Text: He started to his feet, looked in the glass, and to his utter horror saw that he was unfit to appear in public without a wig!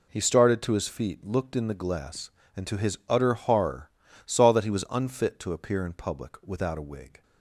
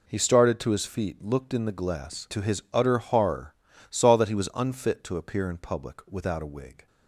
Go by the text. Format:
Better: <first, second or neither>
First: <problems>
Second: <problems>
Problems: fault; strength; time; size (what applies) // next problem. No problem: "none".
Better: first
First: pauses between "horror" and "saw"; slight; at 3.9 s; 0.34 s long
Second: skips "and"; at 2.2 s // pauses between "horror" and "saw"; slight; at 3.5 s; 0.34 s long